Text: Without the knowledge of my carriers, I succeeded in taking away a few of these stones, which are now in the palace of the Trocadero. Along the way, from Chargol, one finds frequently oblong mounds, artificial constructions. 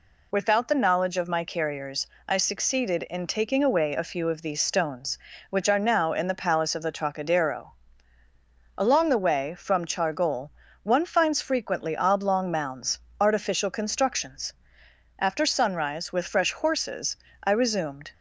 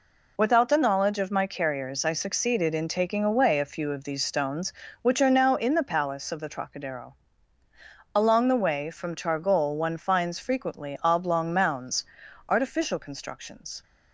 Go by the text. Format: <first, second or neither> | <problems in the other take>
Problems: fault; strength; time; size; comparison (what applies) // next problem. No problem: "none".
second | goes on to say "After sunrise with fresh horses I resumed"; strong; from 15.1 s on; 2.9 s long